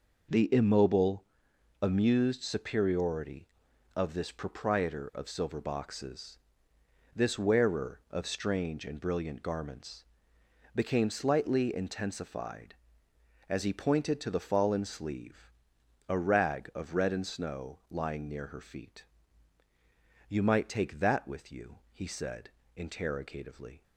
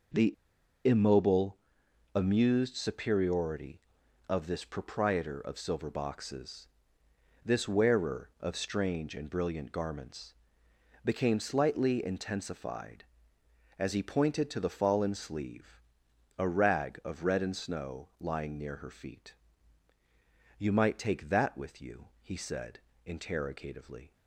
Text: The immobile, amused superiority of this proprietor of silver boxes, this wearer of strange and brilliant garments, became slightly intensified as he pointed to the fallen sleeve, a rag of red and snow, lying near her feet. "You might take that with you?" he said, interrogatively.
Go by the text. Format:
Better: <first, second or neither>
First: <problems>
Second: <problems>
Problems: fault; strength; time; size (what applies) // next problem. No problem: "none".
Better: first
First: none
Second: pauses between "The" and "immobile"; noticeable; at 0.3 s; 0.56 s long